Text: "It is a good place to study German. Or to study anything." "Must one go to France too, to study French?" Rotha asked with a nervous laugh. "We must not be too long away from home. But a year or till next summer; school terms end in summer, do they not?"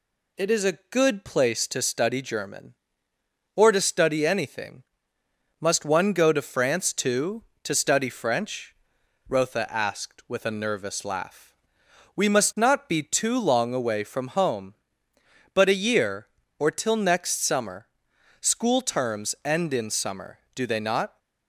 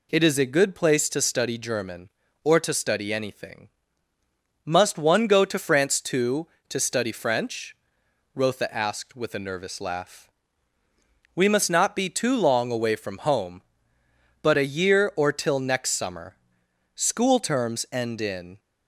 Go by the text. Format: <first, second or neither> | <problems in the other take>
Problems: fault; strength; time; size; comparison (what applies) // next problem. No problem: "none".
first | stops before "summer do they not"; at 18.5 s